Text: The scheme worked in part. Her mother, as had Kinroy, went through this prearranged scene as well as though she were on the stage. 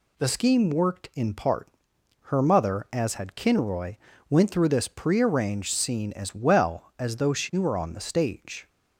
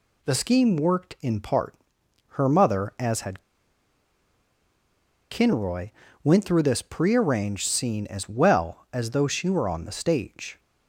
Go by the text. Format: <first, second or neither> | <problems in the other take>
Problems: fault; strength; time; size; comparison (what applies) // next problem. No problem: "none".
first | pauses between "had" and "Kinroy"; strong; at 3.4 s; 1.8 s long